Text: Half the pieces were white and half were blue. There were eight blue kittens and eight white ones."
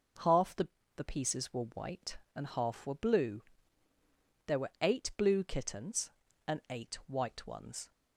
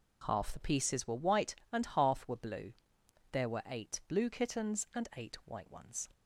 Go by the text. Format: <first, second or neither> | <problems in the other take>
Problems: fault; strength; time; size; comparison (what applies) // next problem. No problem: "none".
second | says "the" twice; at 0.9 s